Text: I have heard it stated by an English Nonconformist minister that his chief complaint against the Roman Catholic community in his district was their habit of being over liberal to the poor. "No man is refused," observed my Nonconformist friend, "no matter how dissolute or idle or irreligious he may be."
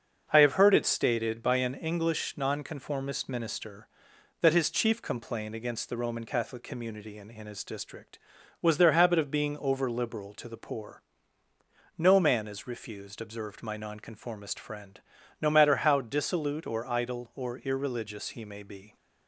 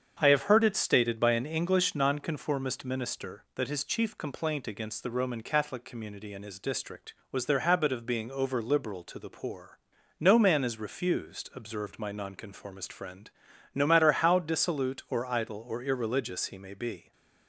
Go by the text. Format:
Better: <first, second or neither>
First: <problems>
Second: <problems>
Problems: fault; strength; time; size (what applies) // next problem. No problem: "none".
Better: second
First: starts louder than the rest; until 1.3 s; 6.5 dB // says "in" twice; at 7.2 s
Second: starts louder than the rest; strong; until 1.2 s; 7.5 dB